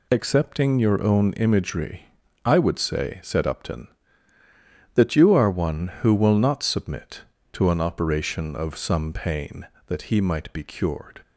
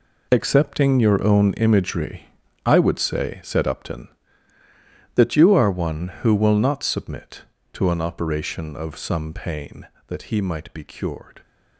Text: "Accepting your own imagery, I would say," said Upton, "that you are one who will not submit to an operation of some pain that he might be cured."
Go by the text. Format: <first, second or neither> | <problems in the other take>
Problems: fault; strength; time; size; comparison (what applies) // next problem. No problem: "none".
first | gets quieter; strong; throughout; 11 dB